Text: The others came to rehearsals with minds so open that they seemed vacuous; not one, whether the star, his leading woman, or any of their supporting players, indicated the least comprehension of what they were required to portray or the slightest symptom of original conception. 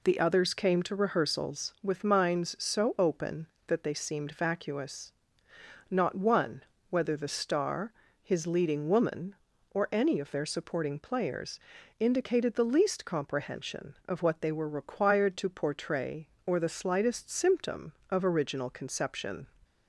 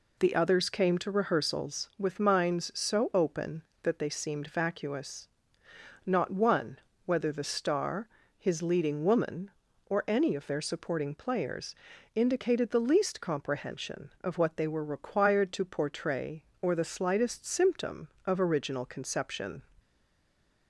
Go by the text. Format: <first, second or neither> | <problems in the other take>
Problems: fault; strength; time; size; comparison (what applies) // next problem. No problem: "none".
first | stays silent after the last word; slight; from 19.7 s on; 0.9 s long